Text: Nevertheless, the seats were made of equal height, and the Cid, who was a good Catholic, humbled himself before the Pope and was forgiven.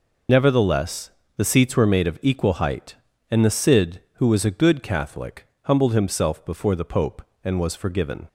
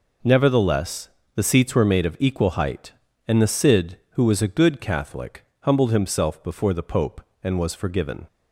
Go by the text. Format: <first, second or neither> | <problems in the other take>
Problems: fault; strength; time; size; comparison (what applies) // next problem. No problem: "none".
second | loses the start of "Nevertheless"; at 0.2 s; 55 ms